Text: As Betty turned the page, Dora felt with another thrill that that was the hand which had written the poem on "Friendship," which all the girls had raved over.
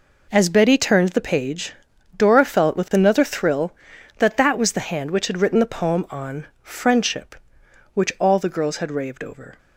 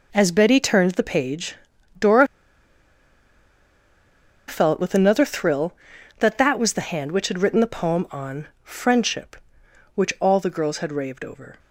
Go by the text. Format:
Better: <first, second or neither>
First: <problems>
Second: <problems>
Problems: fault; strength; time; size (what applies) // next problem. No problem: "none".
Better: first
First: pauses between "on" and "Friendship"; slight; at 6.4 s; 0.16 s long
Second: pauses between "Dora" and "felt"; strong; at 2.2 s; 2.2 s long // pauses between "on" and "Friendship"; slight; at 8.4 s; 0.16 s long